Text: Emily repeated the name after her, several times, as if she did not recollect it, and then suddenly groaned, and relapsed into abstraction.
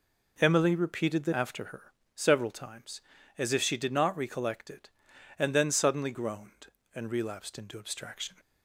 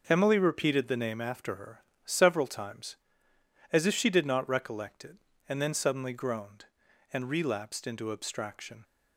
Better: second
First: skips "name"; at 1.3 s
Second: none

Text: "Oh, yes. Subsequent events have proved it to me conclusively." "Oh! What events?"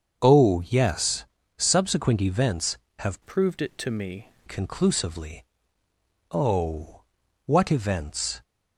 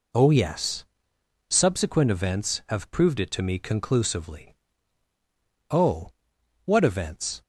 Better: second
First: starts louder than the rest; until 1.2 s; 6.5 dB // changes voice from "proved" to "me"; from 3.2 to 4.2 s; 1.0 s long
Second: none

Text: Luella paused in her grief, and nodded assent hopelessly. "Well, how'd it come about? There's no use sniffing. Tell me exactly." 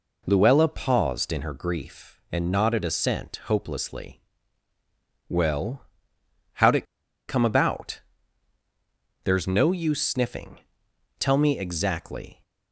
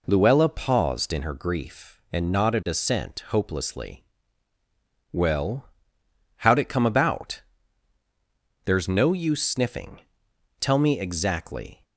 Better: second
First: pauses between "it" and "come"; at 6.8 s; 0.43 s long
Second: none

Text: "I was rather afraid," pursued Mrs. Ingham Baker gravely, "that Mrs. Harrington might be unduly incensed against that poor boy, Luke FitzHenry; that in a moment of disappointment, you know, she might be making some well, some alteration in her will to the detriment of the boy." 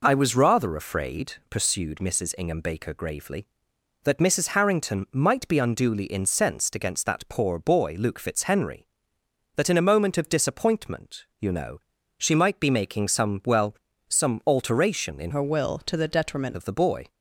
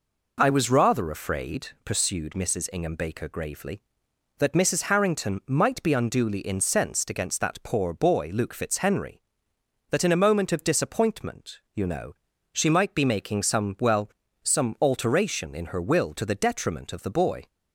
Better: second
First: changes voice from "her" to "detriment"; from 15.3 to 16.5 s; 1.2 s long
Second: none

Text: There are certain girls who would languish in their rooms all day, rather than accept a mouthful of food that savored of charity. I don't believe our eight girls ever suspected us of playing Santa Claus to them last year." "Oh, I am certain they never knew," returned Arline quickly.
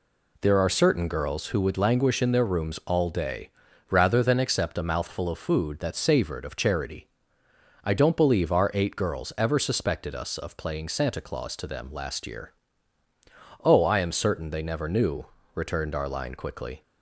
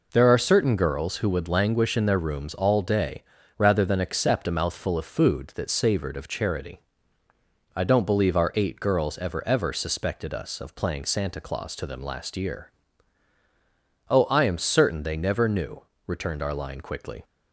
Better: first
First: none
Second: says "ever" twice; at 9.4 s

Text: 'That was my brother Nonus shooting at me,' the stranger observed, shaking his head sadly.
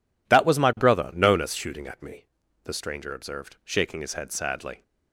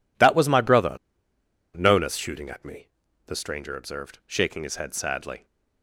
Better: first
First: none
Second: pauses between "brother" and "Nonus"; noticeable; at 0.9 s; 0.80 s long

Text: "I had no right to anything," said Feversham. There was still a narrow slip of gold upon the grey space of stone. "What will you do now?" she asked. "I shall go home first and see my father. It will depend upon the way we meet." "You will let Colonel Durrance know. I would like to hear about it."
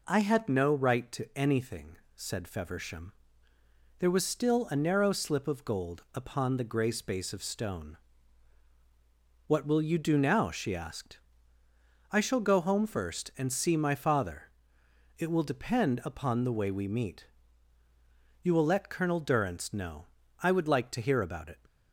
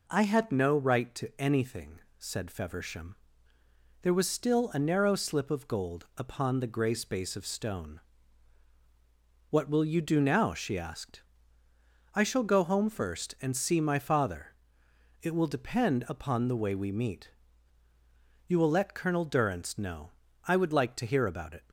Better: neither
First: none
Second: none

